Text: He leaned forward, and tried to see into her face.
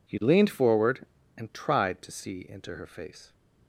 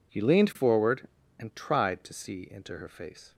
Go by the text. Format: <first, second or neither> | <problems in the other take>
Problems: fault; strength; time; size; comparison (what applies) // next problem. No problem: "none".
neither | none